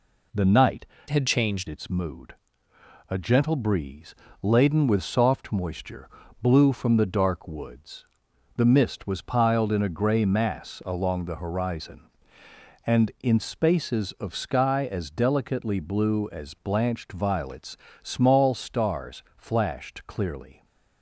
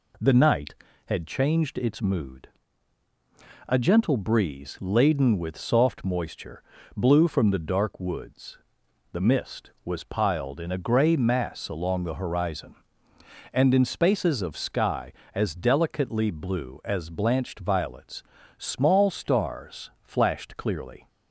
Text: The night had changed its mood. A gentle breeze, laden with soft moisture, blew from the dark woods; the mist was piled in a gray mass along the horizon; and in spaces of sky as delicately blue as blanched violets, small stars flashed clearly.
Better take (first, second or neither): second